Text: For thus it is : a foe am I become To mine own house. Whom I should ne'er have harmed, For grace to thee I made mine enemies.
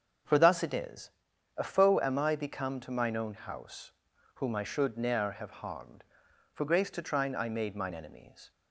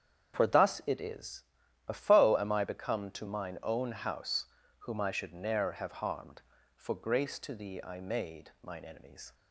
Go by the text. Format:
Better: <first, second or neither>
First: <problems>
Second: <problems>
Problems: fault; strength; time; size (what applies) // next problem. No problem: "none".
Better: second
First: starts louder than the rest; until 1.7 s; 7 dB // says "trine" for "thee"; at 7.0 s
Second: starts louder than the rest; strong; until 1.3 s; 8 dB